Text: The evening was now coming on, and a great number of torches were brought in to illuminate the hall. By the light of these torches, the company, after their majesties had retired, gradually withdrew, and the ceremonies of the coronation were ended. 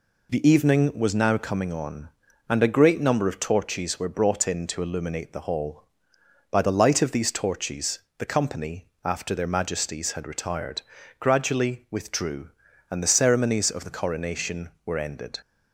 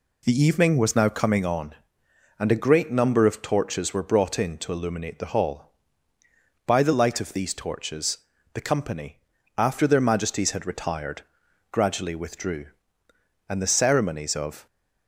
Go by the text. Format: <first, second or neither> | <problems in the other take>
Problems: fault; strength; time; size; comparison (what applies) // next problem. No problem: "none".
first | stops before "the coronation were ended"; at 14.6 s